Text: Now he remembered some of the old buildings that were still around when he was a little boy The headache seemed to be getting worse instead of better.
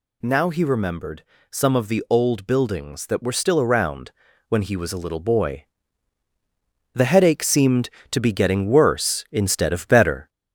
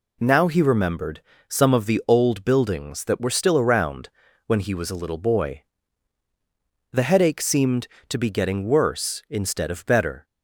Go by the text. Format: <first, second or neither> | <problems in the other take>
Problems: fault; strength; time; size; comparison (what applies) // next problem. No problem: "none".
second | gets louder; slight; throughout; 3 dB // pauses between "remembered" and "some"; slight; at 1.2 s; 0.28 s long; slight in the second // pauses between "around" and "when"; at 4.1 s; 0.38 s long; also in the second // pauses between "boy" and "The"; strong; at 5.6 s; 1.2 s long; strong in the second